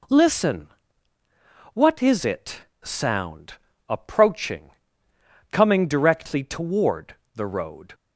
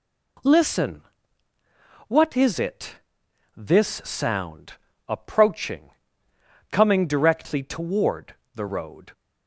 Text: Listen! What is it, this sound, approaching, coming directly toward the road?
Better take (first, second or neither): second